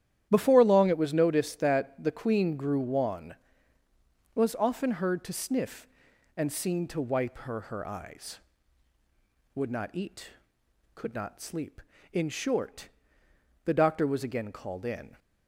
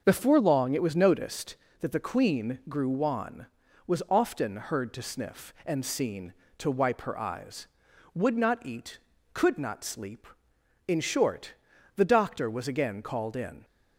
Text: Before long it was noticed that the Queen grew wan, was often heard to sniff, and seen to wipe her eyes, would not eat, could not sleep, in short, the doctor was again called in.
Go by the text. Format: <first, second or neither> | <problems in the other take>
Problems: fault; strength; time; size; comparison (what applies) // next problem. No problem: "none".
second | starts louder than the rest; strong; until 1.3 s; 11 dB; also in the second // says "her" twice; at 7.6 s